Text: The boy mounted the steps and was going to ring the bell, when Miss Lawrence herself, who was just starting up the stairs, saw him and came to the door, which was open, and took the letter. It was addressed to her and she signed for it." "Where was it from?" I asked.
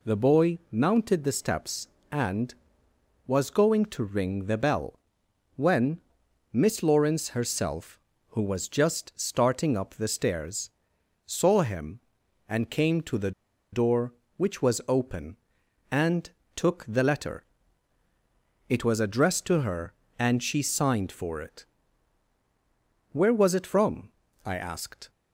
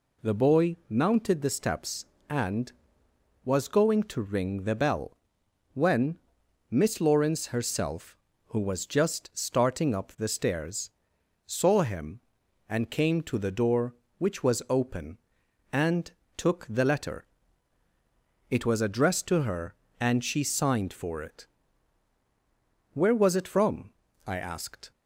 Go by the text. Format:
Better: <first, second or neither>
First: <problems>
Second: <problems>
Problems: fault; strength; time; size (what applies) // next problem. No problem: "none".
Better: second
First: pauses between "when" and "Miss"; noticeable; at 5.9 s; 0.54 s long // pauses between "the" and "door"; at 13.3 s; 0.41 s long // pauses between "and" and "took"; slight; at 16.2 s; 0.26 s long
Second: pauses between "when" and "Miss"; noticeable; at 6.1 s; 0.54 s long // pauses between "and" and "took"; slight; at 16.1 s; 0.26 s long